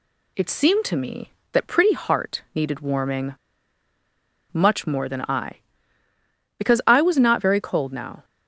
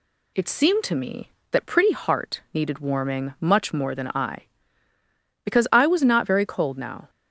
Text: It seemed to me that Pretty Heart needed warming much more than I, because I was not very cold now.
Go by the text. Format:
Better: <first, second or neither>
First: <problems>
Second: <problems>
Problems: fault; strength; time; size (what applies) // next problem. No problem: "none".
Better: second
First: pauses between "warming" and "much"; at 3.3 s; 1.1 s long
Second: none